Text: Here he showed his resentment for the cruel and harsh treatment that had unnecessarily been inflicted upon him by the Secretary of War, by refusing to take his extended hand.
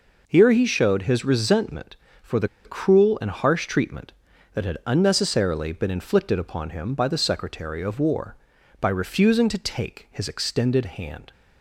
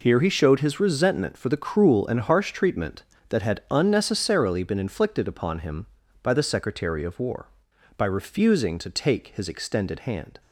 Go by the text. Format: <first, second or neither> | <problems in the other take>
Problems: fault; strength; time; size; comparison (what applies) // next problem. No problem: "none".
second | pauses between "the" and "cruel"; slight; at 2.4 s; 0.17 s long